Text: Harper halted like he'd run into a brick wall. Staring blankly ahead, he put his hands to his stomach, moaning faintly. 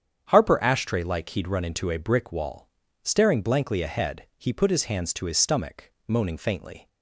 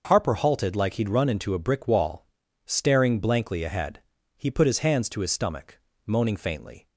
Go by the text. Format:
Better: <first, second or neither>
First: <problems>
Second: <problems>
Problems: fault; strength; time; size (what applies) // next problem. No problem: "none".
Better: second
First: starts louder than the rest; strong; until 1.3 s; 8.5 dB // says "ashtray" for "halted"; at 0.5 s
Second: starts louder than the rest; until 1.0 s; 6 dB